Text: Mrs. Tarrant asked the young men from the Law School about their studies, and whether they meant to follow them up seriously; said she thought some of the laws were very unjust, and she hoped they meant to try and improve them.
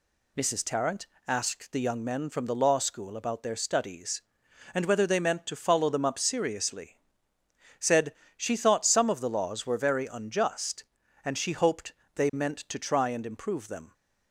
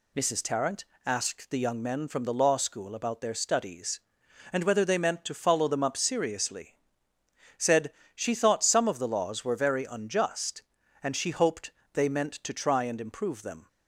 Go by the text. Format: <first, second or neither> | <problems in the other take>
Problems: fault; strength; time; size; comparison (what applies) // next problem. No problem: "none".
neither | pauses between "Tarrant" and "asked"; slight; the same in both // pauses between "said" and "she"; slight; the same in both // pauses between "hoped" and "they"; slight; the same in both